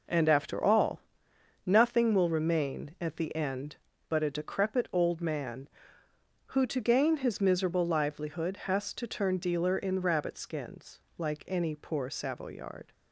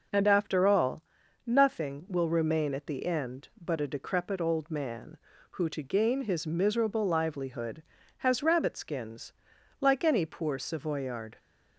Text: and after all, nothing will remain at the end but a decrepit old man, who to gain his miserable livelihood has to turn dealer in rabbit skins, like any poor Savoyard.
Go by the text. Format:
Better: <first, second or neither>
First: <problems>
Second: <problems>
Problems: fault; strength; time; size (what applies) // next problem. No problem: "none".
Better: first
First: none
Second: skips "to turn dealer in"; at 8.4 s